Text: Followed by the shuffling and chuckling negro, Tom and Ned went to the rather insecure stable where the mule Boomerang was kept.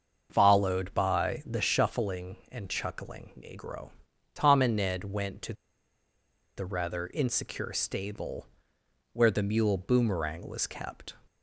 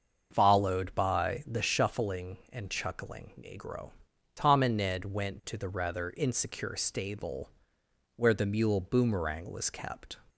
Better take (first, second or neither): second